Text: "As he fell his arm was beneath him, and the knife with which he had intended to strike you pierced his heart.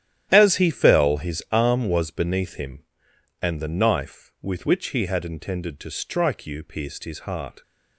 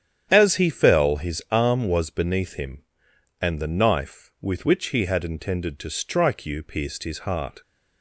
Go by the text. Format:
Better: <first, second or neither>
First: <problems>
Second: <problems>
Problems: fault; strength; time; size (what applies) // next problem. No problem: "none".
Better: second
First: gets quieter; strong; throughout; 13 dB // starts louder than the rest; strong; until 1.3 s; 11 dB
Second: starts louder than the rest; strong; until 1.3 s; 9 dB